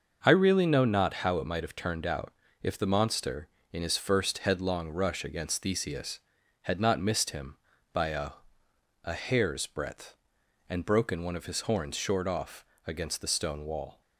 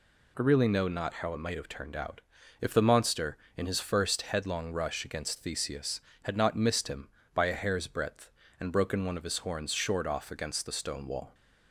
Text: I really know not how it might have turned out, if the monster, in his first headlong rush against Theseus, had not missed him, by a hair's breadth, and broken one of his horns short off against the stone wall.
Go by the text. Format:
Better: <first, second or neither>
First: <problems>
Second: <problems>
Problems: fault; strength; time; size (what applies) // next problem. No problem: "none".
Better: second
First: starts louder than the rest; until 1.2 s; 6.5 dB // says "a" twice; at 9.0 s // pauses between "off" and "against"; slight; at 12.6 s; 0.24 s long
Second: none